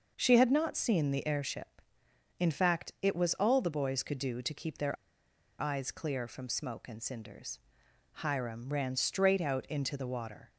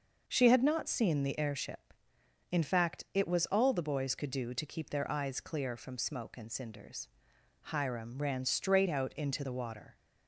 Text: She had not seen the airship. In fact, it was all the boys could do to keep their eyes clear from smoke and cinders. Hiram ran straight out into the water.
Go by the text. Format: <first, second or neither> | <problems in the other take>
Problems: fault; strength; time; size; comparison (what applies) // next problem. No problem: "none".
second | pauses between "their" and "eyes"; noticeable; at 4.9 s; 0.65 s long